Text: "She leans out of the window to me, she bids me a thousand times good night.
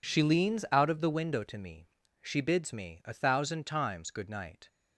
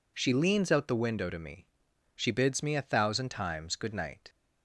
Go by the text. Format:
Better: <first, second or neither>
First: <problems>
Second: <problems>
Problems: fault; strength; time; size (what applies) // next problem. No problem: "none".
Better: first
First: none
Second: skips "of"; at 0.8 s